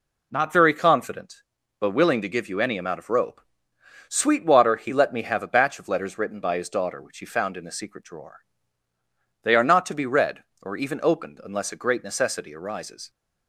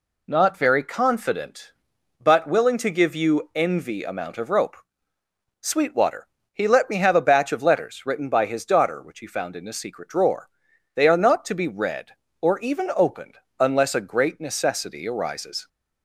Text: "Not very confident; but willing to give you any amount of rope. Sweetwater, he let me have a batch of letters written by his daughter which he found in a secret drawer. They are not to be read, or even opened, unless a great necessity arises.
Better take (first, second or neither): first